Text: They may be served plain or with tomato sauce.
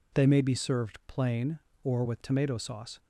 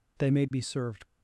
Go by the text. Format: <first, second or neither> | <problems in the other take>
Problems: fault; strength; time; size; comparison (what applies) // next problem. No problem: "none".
first | stops before "plain or with tomato sauce"; at 1.0 s